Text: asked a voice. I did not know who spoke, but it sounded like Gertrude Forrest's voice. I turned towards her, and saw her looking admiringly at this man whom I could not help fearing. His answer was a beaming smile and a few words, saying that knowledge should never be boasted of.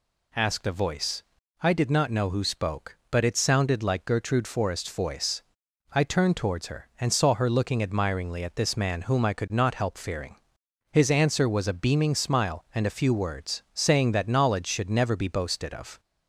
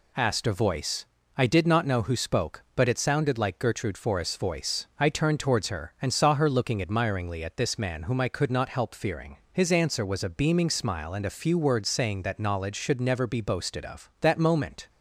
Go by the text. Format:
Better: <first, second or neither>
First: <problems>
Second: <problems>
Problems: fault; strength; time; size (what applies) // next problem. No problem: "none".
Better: first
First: none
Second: goes on to say "That moment"; noticeable; from 14.1 s on; 0.70 s long